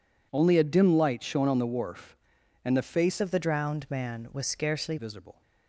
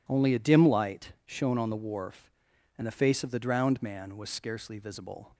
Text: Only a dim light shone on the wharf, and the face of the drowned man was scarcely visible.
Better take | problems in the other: second | changes voice from "of" to "scarcely"; from 3.2 to 4.9 s; 1.7 s long

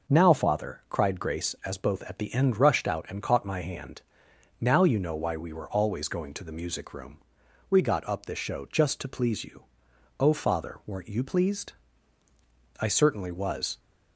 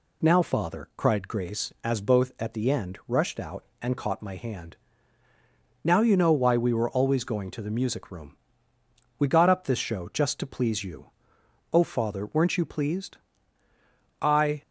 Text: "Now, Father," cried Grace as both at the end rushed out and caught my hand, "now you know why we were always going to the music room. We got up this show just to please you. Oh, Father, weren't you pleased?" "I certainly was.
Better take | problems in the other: first | stops before "certainly was"; at 14.6 s

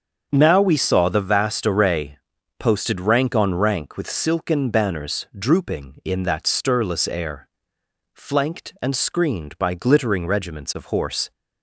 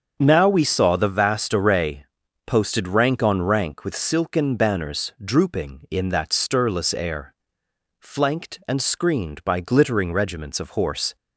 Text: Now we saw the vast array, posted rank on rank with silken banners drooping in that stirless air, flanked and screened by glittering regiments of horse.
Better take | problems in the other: neither | starts louder than the rest; the same in both

